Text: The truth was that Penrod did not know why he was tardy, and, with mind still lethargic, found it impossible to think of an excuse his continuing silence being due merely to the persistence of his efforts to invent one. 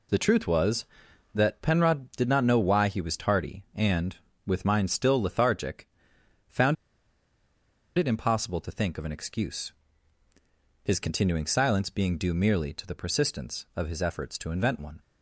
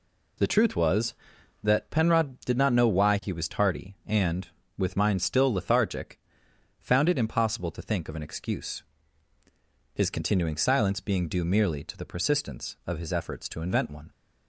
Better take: second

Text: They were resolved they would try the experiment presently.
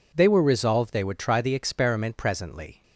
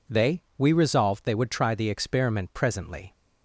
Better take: first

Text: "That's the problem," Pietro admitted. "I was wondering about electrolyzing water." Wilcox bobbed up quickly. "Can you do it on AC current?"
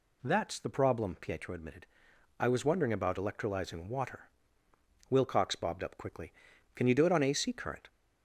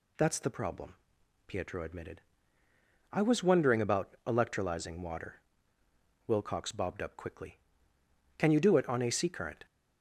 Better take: neither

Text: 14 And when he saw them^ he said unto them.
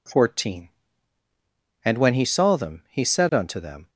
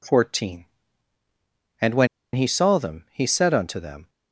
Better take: first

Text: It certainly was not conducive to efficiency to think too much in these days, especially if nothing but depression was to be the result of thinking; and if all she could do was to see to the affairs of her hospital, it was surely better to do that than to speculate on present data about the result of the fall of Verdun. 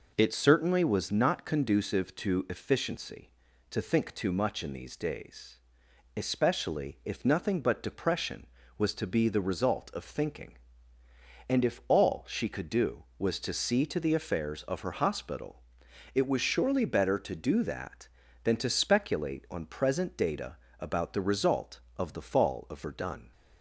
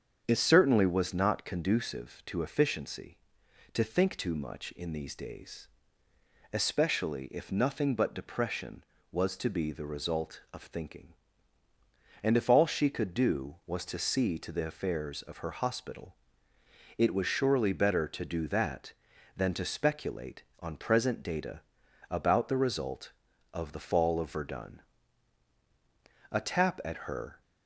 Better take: first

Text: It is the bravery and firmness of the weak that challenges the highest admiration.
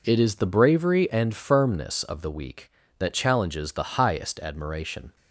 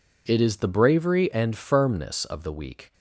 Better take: first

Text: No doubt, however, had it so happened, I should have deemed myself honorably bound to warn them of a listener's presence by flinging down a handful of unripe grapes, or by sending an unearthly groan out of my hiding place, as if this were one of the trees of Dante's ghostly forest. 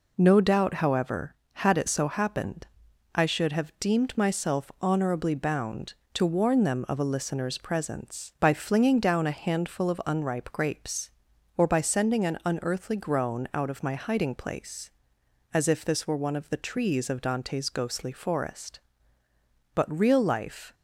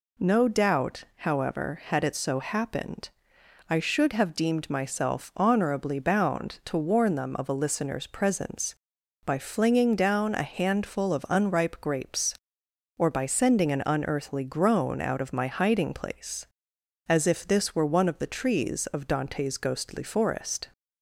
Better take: second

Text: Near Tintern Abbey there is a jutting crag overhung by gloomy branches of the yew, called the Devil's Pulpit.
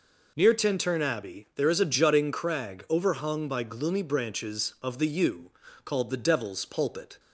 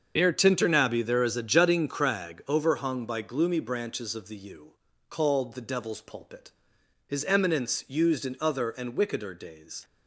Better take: first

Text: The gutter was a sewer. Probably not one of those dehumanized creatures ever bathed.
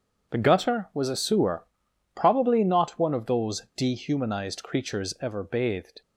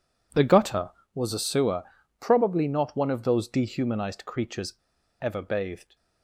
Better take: first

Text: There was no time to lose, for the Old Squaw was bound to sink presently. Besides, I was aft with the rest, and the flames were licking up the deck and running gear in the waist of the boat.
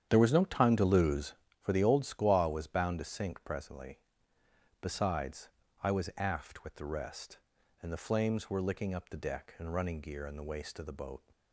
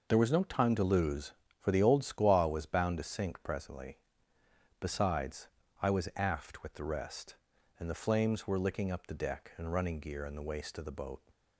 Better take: second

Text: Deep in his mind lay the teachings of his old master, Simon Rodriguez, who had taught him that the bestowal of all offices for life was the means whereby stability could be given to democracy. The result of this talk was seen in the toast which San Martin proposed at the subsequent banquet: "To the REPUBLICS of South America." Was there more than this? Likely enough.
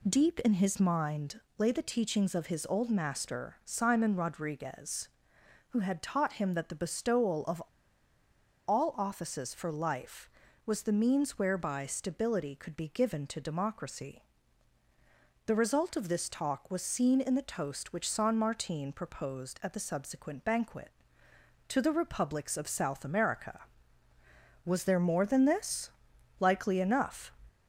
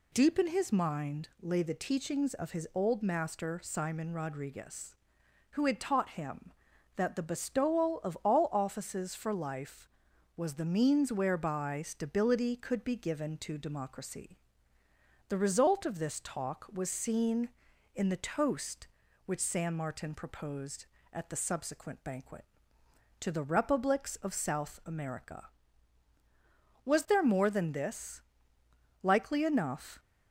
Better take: second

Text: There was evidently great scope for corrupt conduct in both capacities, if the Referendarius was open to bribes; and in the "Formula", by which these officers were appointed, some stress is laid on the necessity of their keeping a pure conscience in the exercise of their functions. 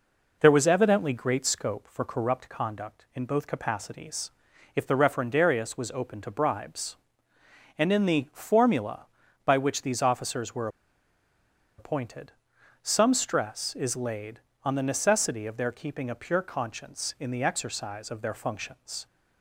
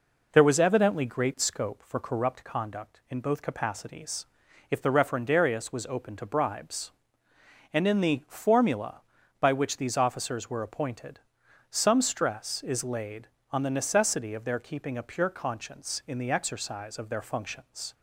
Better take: second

